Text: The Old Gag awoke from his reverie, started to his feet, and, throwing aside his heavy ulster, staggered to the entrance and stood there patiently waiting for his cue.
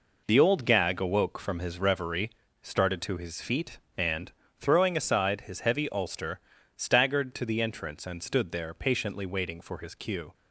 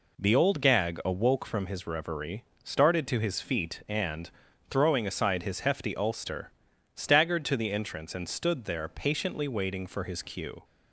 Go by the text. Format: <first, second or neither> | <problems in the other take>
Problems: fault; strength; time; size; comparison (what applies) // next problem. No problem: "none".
first | says "hefty" for "heavy"; at 5.6 s